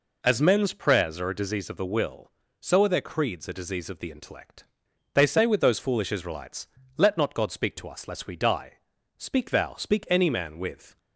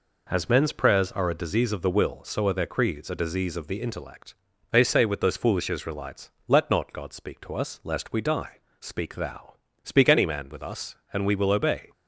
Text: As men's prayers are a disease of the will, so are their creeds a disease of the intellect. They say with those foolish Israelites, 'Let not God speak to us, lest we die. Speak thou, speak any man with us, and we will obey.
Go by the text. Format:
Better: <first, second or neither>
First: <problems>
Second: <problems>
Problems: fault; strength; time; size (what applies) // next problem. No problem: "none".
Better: second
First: stops before "us and we will obey"; at 10.9 s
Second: none